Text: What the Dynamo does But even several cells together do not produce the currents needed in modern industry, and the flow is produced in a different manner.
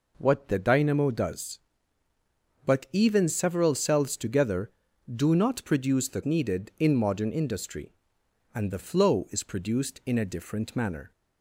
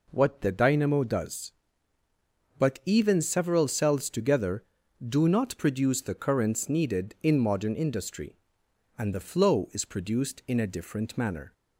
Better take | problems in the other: second | skips "currents"; at 6.2 s

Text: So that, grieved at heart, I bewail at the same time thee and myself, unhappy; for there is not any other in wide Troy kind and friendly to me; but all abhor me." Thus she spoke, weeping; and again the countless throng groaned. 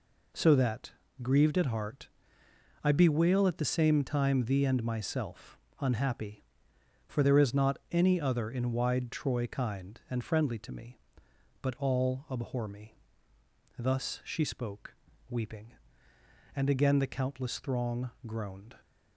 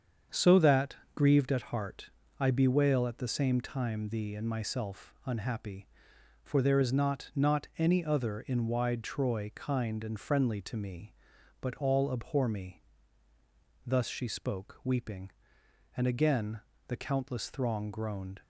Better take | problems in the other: first | starts louder than the rest; strong; until 1.5 s; 7.5 dB // says "not" twice; at 7.3 s // pauses between "again" and "the"; slight; at 16.5 s; 0.28 s long

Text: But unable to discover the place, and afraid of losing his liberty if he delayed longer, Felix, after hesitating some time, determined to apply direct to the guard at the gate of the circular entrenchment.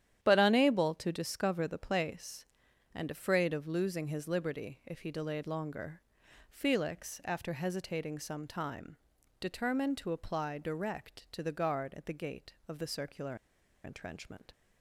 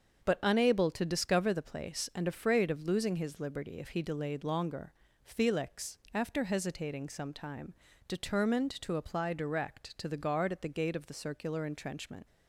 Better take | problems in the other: second | starts louder than the rest; strong; until 1.2 s; 10.5 dB; also in the second // pauses between "circular" and "entrenchment"; noticeable; at 13.3 s; 0.49 s long

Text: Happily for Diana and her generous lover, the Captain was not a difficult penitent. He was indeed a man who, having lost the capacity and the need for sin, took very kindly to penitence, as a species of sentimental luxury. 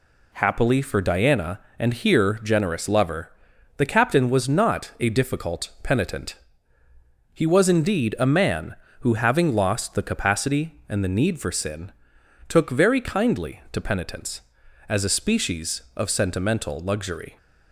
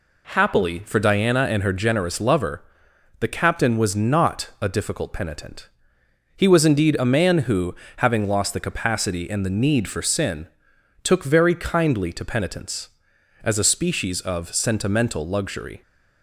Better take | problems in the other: second | says "here" for "her"; at 1.9 s

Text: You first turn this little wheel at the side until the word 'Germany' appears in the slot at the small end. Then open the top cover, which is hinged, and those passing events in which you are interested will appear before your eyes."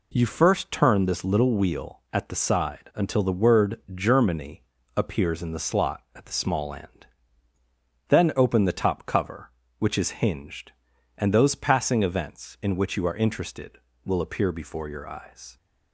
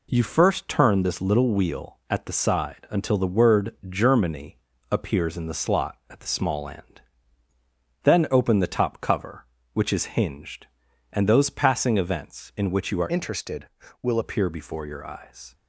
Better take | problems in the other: first | pauses between "Germany" and "appears"; slight; at 4.5 s; 0.32 s long; slight in the first // changes voice from "interested" to "will"; from 13.1 to 14.1 s; 1.0 s long

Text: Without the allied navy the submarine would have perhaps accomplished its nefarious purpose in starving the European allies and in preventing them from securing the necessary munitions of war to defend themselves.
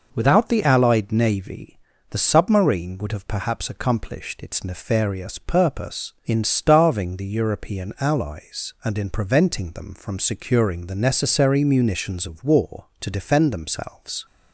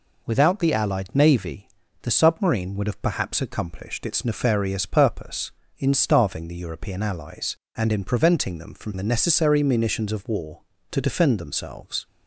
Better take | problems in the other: first | pauses between "navy" and "the"; slight; at 1.6 s; 0.36 s long; slight in the first // skips "securing"; at 8.9 s

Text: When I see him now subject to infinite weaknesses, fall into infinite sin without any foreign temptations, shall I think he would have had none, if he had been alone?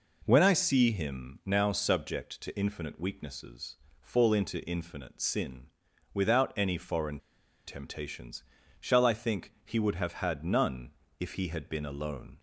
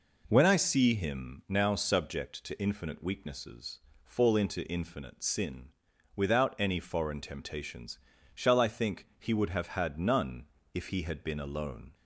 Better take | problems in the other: second | pauses between "sin" and "without"; noticeable; at 5.6 s; 0.46 s long; noticeable in the second // pauses between "foreign" and "temptations"; noticeable; at 7.1 s; 0.48 s long

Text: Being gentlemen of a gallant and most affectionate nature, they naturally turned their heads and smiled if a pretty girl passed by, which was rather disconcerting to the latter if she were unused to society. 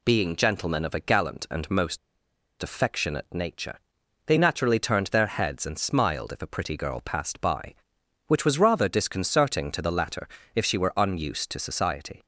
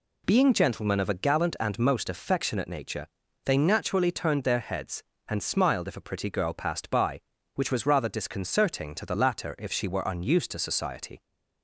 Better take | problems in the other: second | pauses between "most" and "affectionate"; noticeable; at 1.9 s; 0.64 s long // pauses between "latter" and "if"; slight; at 10.2 s; 0.28 s long

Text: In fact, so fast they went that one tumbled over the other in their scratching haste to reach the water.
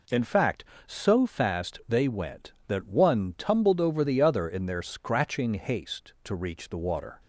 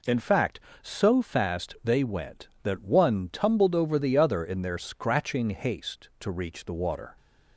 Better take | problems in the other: neither | none

